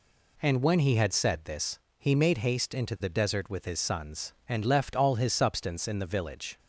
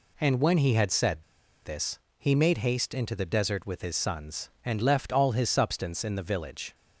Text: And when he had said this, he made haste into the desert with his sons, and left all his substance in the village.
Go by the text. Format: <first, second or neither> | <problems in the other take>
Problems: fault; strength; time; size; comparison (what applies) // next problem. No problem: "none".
first | pauses between "said" and "this"; at 1.2 s; 0.42 s long